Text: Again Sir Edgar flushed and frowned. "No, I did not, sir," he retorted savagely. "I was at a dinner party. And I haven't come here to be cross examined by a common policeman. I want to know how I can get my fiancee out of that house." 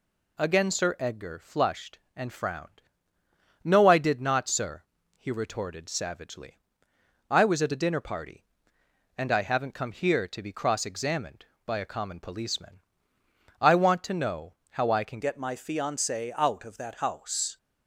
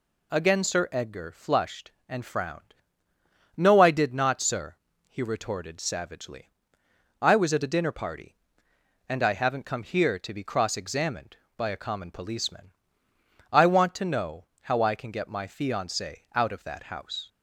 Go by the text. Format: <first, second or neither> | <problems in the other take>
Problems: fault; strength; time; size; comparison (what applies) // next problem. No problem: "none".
second | pauses between "know" and "how"; slight; at 14.5 s; 0.16 s long; slight in the second // changes voice at "get"; from 15.2 s on; 2.3 s long